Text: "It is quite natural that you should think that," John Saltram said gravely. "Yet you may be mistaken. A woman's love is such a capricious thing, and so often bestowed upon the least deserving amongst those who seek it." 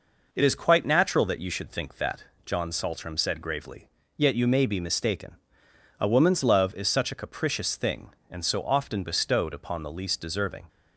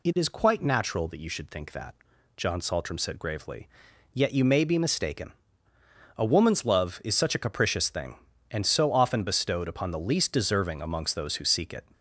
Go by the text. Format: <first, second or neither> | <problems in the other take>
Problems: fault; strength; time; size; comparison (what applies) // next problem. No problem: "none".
second | stops before "amongst those who seek it"; at 10.6 s